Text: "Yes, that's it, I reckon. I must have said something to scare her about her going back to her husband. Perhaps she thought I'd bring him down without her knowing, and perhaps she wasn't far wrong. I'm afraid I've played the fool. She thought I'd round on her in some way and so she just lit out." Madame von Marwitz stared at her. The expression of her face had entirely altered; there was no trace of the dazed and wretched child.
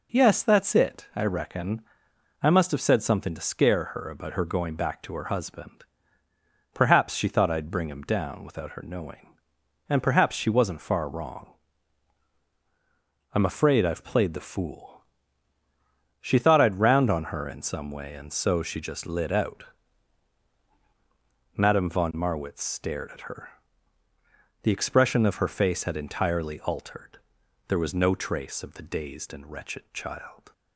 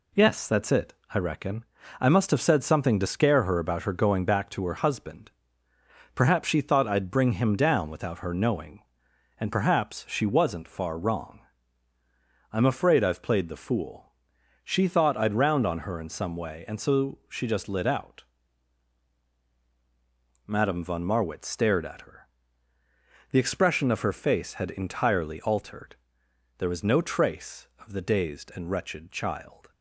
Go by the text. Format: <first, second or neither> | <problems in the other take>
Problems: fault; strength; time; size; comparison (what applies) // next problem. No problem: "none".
neither | none